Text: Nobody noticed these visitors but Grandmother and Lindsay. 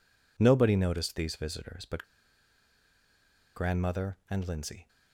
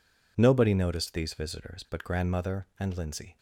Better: second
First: pauses between "but" and "Grandmother"; strong; at 2.0 s; 1.5 s long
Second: none

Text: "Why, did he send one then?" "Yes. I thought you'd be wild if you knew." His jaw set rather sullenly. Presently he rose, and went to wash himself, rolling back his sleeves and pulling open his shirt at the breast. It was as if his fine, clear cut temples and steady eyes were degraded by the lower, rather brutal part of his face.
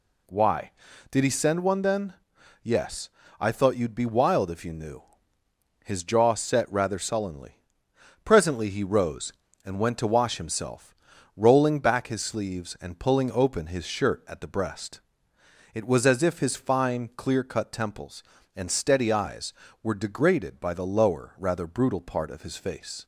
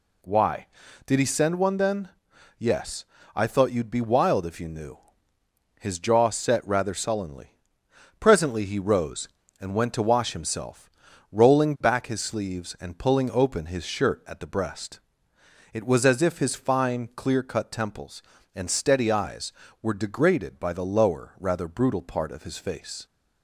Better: neither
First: none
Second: none

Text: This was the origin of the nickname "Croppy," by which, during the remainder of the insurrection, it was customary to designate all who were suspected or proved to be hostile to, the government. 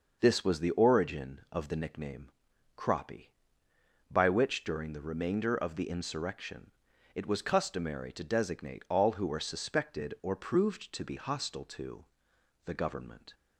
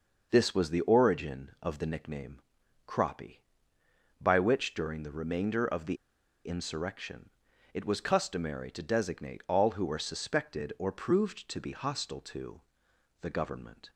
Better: first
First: pauses between "nickname" and "Croppy"; noticeable; at 2.2 s; 0.46 s long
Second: pauses between "nickname" and "Croppy"; noticeable; at 2.3 s; 0.46 s long // pauses between "the" and "insurrection"; noticeable; at 5.9 s; 0.51 s long

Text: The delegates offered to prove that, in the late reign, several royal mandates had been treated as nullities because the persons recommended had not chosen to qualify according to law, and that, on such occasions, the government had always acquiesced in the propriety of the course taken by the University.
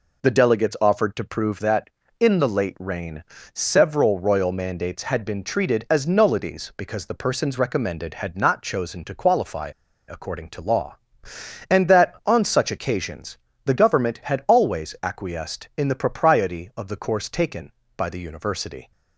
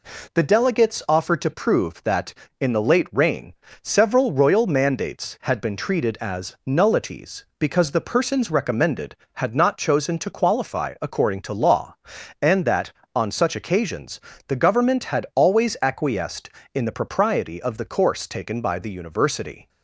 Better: second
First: pauses between "qualify" and "according"; at 9.6 s; 0.41 s long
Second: none

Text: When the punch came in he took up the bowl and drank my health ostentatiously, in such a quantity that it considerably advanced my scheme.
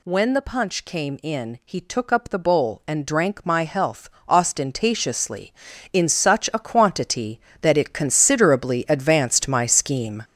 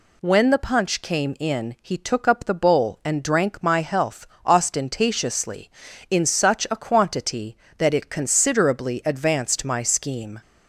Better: second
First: gets louder; strong; throughout; 8.5 dB // pauses between "health" and "ostentatiously"; slight; at 4.0 s; 0.18 s long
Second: pauses between "health" and "ostentatiously"; slight; at 4.2 s; 0.18 s long

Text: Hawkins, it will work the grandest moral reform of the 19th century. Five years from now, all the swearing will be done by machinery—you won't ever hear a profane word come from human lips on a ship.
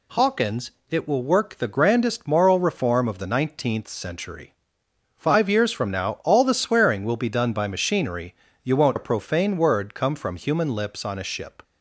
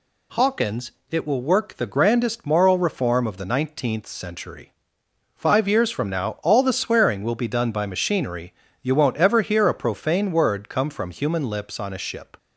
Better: second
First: skips "ever hear"; at 8.9 s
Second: none

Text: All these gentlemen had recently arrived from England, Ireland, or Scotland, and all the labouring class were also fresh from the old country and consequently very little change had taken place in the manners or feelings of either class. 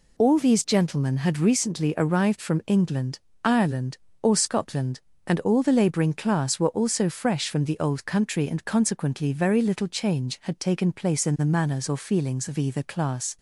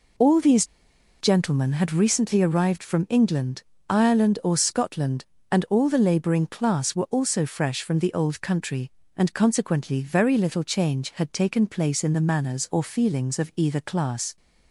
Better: first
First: none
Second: pauses between "these" and "gentlemen"; noticeable; at 0.6 s; 0.55 s long

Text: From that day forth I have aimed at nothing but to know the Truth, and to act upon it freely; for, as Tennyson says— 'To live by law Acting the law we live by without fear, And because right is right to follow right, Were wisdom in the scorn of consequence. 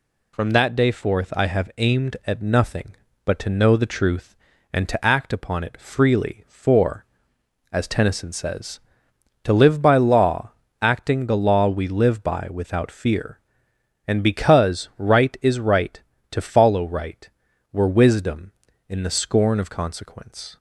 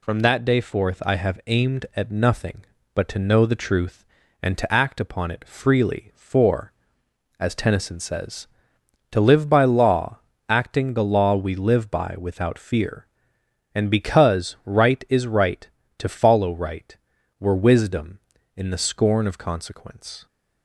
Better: neither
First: pauses between "law" and "Acting"; slight; at 10.5 s; 0.32 s long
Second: pauses between "law" and "Acting"; slight; at 10.1 s; 0.32 s long

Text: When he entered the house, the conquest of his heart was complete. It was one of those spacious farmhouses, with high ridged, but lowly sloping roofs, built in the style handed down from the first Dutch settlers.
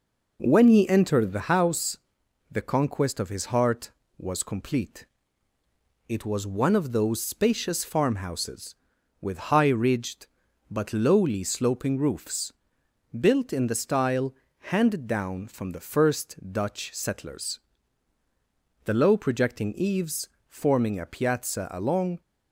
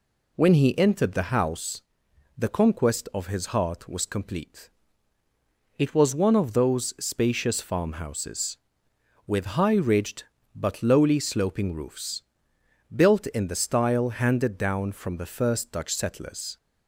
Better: second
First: pauses between "style" and "handed"; slight; at 14.3 s; 0.36 s long // goes on to say "The low projecting eaves forming a piazza along"; strong; from 18.8 s on; 3.3 s long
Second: none

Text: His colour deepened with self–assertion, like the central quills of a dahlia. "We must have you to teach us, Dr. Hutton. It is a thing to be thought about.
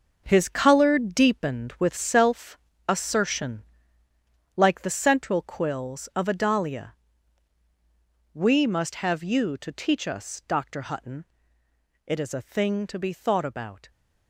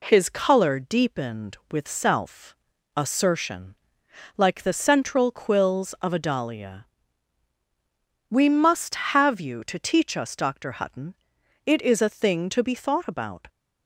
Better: second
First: gets quieter; strong; throughout; 10 dB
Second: none

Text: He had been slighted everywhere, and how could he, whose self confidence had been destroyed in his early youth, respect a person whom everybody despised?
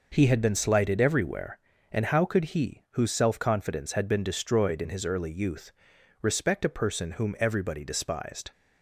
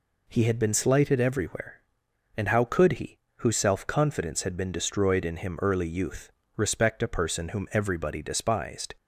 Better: first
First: none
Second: says "him" for "his"; at 5.3 s

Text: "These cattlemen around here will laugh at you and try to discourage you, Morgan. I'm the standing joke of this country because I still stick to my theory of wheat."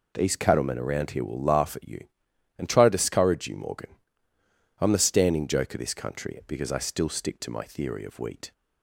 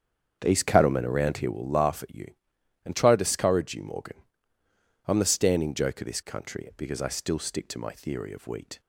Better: first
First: none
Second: starts louder than the rest; strong; until 1.7 s; 7.5 dB

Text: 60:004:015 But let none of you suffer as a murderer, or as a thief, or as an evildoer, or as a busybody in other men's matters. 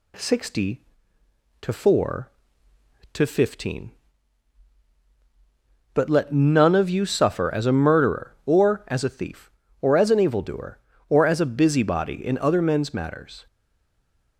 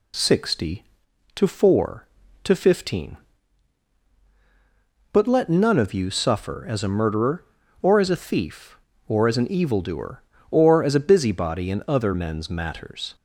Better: second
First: stays silent after the last word; slight; from 13.4 s on; 0.9 s long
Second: none

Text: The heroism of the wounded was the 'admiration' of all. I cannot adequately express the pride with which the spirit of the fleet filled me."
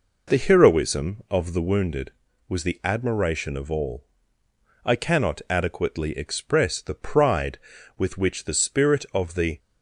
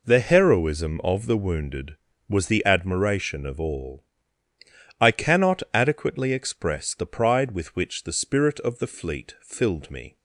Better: second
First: stops before "fleet filled me"; at 9.5 s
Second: none

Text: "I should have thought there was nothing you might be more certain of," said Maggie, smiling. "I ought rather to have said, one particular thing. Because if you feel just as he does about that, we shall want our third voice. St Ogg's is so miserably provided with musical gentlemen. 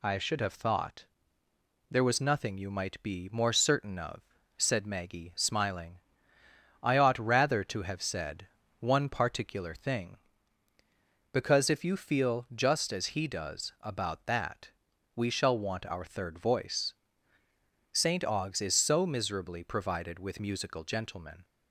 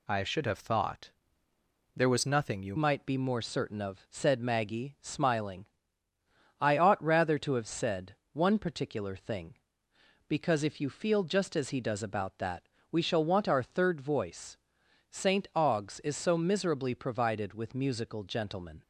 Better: first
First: pauses between "thought" and "there"; noticeable; at 1.0 s; 0.86 s long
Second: pauses between "thought" and "there"; noticeable; at 1.1 s; 0.86 s long // changes voice at "might"; from 2.7 s on; 16.1 s long

